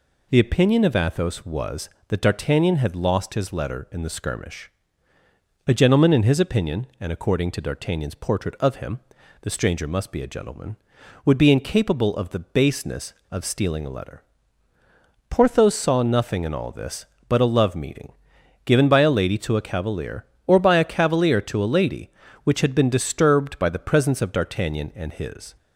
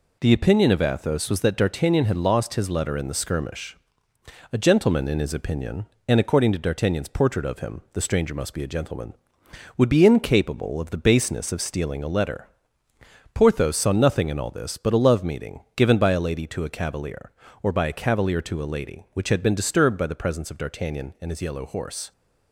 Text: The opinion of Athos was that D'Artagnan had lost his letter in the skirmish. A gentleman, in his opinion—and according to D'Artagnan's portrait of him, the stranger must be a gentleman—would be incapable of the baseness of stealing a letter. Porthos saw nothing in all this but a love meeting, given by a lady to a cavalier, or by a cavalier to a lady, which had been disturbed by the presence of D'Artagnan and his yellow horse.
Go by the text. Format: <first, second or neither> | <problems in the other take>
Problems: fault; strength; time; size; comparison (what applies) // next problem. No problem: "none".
second | stops before "yellow horse"; at 25.5 s